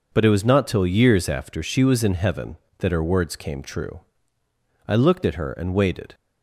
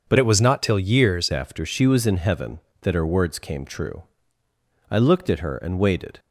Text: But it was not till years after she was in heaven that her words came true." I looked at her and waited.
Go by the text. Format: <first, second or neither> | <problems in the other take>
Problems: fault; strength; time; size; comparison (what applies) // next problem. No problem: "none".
first | changes voice from "it" to "years"; from 0.1 to 1.2 s; 1.1 s long